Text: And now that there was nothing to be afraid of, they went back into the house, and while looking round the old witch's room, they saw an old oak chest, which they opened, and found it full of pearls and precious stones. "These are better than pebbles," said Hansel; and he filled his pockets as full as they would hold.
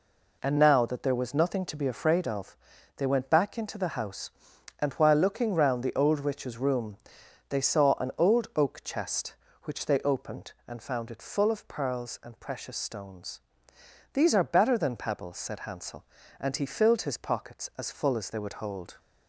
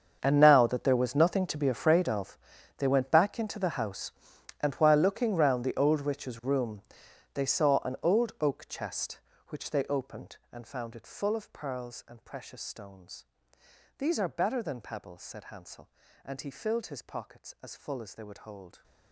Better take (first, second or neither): first